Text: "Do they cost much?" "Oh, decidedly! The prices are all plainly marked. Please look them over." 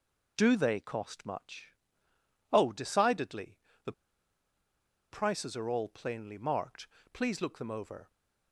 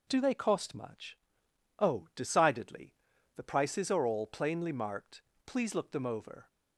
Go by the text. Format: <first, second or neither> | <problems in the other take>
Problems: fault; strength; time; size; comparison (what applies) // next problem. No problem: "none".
second | pauses between "The" and "prices"; at 3.9 s; 1.2 s long